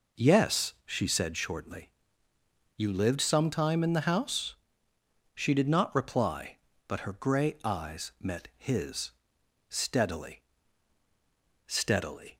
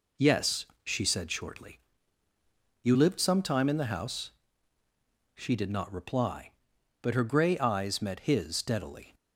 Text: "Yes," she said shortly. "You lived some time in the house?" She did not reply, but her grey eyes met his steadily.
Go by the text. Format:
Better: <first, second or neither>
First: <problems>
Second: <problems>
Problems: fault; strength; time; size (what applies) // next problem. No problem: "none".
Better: second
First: pauses between "his" and "steadily"; noticeable; at 9.1 s; 0.58 s long // says "steadily" twice; at 11.6 s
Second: none